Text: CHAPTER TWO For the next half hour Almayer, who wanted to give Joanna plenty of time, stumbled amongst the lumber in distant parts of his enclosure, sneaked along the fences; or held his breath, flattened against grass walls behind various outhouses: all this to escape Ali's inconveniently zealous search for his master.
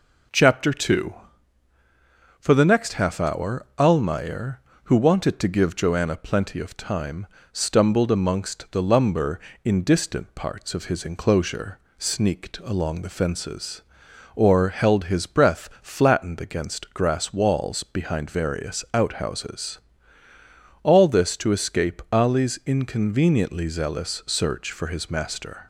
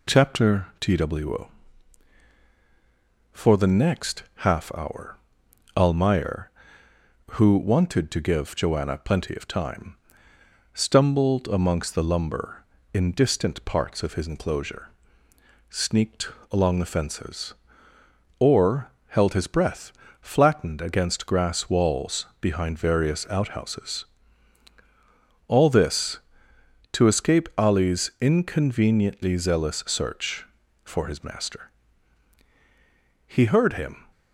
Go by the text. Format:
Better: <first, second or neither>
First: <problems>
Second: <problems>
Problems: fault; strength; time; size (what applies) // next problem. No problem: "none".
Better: first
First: none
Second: pauses between "hour" and "Almayer"; noticeable; at 5.1 s; 0.58 s long // pauses between "sneaked" and "along"; slight; at 16.3 s; 0.20 s long // pauses between "or" and "held"; slight; at 18.8 s; 0.20 s long // pauses between "walls" and "behind"; slight; at 22.2 s; 0.16 s long // goes on to say "He heard him"; noticeable; from 33.2 s on; 0.80 s long